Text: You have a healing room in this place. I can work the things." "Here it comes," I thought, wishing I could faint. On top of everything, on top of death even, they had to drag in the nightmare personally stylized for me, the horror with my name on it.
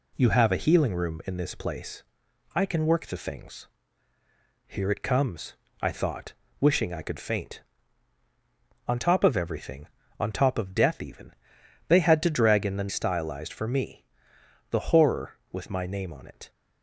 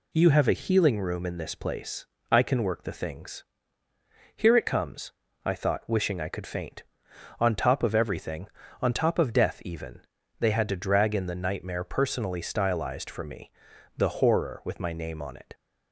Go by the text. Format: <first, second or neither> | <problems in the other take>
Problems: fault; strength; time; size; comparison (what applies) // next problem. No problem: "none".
second | skips "nightmare personally"; at 12.8 s